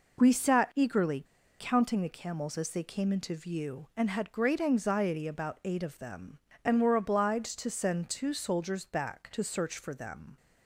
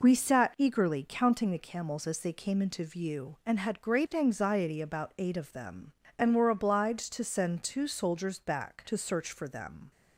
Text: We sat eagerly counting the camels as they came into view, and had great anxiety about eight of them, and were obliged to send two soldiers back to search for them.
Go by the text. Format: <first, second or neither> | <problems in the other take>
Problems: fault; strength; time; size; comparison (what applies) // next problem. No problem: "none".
second | pauses between "eagerly" and "counting"; at 1.2 s; 0.36 s long